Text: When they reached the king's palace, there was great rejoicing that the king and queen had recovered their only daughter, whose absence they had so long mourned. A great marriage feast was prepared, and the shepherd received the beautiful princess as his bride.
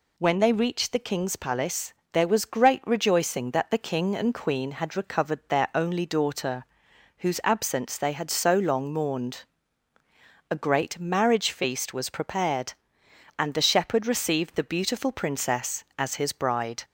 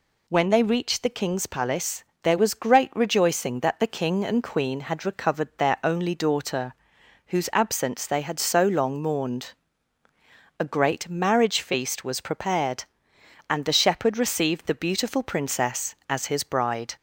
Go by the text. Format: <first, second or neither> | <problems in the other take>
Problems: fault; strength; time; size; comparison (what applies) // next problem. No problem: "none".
neither | none